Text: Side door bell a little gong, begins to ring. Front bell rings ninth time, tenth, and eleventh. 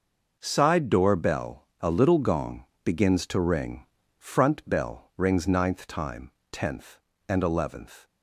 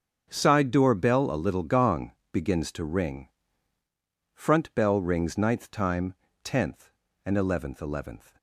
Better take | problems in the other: first | starts louder than the rest; strong; until 1.3 s; 7.5 dB // says "eleventh" twice; at 7.8 s

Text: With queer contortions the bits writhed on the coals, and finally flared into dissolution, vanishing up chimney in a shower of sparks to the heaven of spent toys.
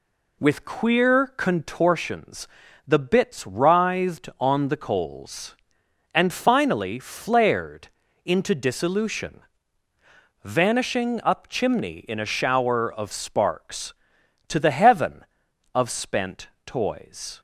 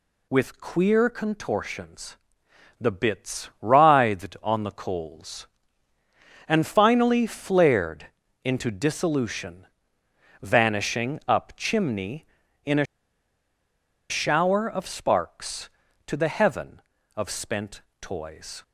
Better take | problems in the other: first | pauses between "contortions" and "the"; noticeable; at 2.1 s; 0.60 s long; also in the first // pauses between "flared" and "into"; slight; at 8.0 s; 0.36 s long; slight in the first // pauses between "a" and "shower"; strong; at 12.8 s; 1.2 s long // pauses between "spent" and "toys"; slight; at 17.8 s; 0.18 s long; slight in the first

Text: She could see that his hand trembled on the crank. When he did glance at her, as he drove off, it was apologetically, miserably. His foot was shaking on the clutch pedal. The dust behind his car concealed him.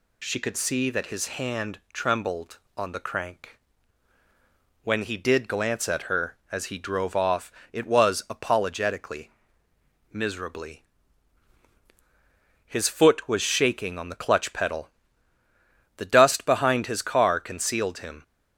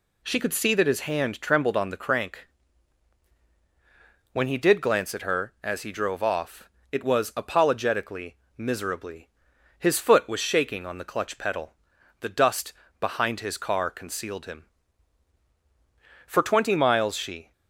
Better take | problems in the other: first | pauses between "dust" and "behind"; slight; at 12.7 s; 0.28 s long // goes on to say "For twenty miles she"; noticeable; from 16.2 s on; 1.2 s long

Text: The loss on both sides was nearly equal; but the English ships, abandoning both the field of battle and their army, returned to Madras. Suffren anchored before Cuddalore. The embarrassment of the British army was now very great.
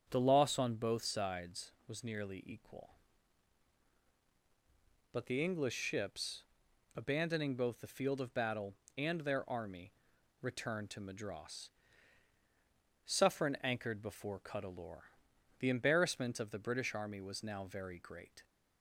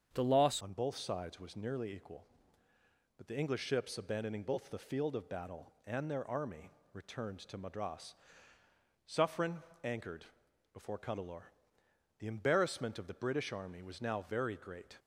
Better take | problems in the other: first | starts louder than the rest; strong; until 1.1 s; 7.5 dB; strong in the first // changes voice at "on"; from 0.6 s on; 14.3 s long // pauses between "Suffren" and "anchored"; slight; at 9.6 s; 0.22 s long // pauses between "anchored" and "before"; noticeable; at 10.2 s; 0.48 s long

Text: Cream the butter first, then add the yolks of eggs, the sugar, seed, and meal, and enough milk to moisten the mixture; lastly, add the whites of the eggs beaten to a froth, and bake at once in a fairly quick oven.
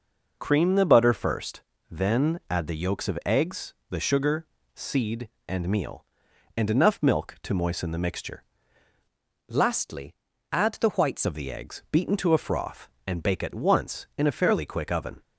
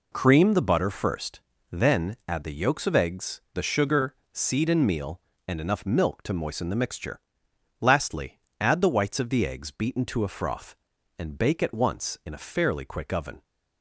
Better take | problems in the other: second | changes voice from "lastly" to "whites"; from 9.4 to 11.2 s; 1.8 s long

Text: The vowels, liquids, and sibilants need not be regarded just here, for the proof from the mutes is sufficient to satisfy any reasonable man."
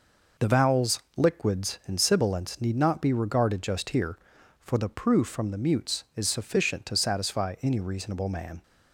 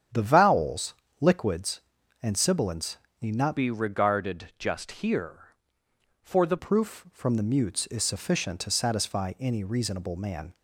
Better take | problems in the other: first | starts louder than the rest; strong; until 1.3 s; 8 dB // pauses between "sibilants" and "need"; slight; at 2.9 s; 0.24 s long // changes voice from "be" to "the"; from 3.5 to 6.5 s; 3.0 s long

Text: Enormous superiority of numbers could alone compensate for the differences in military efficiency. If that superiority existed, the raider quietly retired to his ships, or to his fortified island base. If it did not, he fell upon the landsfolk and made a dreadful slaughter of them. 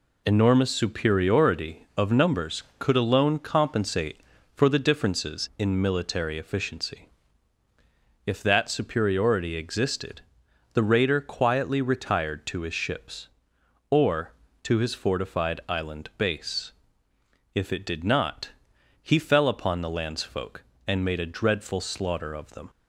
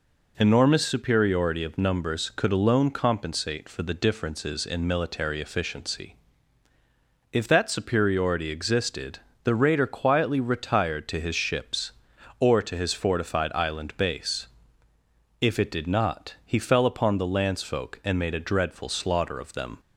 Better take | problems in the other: neither | none

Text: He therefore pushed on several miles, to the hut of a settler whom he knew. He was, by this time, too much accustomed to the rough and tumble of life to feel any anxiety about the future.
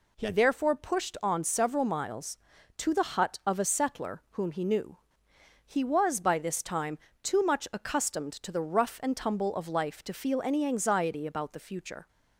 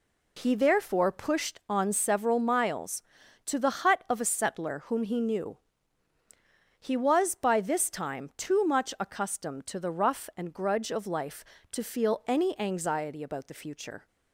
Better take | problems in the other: first | says "grudge" for "tumble"; at 10.5 s

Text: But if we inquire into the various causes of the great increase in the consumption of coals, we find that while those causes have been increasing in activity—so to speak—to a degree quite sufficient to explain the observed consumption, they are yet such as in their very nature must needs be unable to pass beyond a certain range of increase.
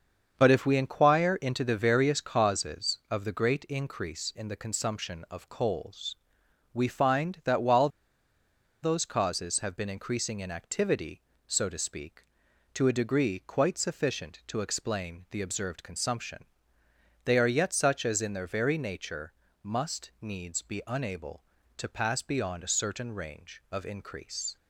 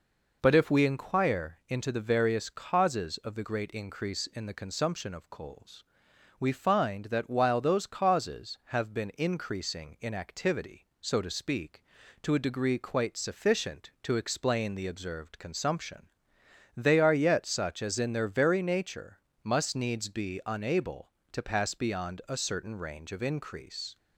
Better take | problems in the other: second | starts louder than the rest; until 1.3 s; 7 dB // pauses between "while" and "those"; noticeable; at 7.8 s; 0.94 s long // pauses between "nature" and "must"; slight; at 19.3 s; 0.32 s long; slight in the second

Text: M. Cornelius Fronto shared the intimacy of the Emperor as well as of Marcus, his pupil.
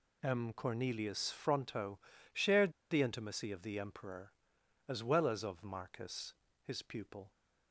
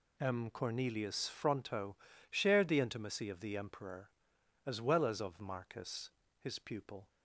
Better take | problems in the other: second | pauses between "Fronto" and "shared"; slight; at 1.9 s; 0.34 s long; slight in the second // pauses between "shared" and "the"; slight; at 2.7 s; 0.19 s long

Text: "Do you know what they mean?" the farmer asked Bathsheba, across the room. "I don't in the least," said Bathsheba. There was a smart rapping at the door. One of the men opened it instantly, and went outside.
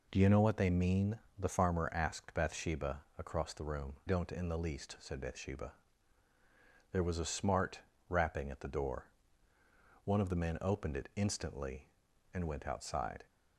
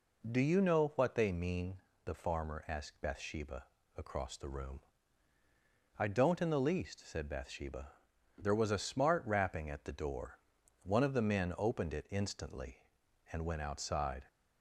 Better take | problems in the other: second | skips "I"; at 4.0 s // pauses between "smart" and "rapping"; slight; at 7.8 s; 0.28 s long

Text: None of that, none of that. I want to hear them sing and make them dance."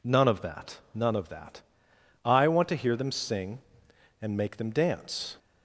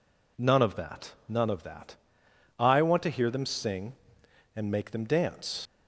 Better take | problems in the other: first | leaves "dance" unfinished; at 5.6 s; 70 ms

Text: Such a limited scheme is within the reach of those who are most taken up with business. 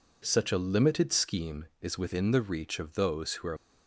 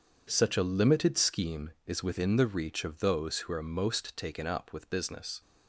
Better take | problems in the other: second | stops before "most taken up with business"; at 3.5 s

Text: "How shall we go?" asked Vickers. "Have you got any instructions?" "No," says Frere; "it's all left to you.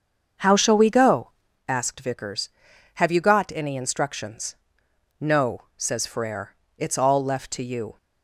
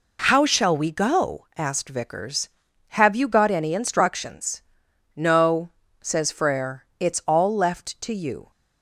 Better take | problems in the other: second | starts louder than the rest; until 1.7 s; 7 dB

